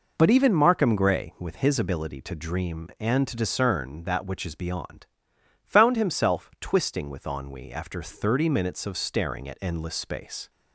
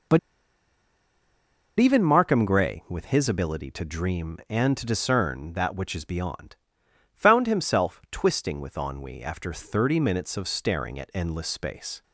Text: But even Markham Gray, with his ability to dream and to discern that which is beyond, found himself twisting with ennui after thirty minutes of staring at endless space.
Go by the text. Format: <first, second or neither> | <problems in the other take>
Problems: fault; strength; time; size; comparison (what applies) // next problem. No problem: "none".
first | pauses between "But" and "even"; strong; at 0.1 s; 1.6 s long